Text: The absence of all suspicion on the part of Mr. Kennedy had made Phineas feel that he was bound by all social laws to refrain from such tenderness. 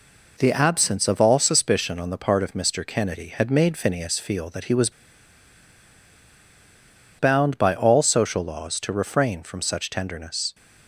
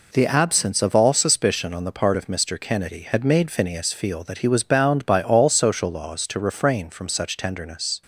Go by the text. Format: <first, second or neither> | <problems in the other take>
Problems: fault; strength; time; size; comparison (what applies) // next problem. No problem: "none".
second | pauses between "was" and "bound"; strong; at 4.9 s; 2.2 s long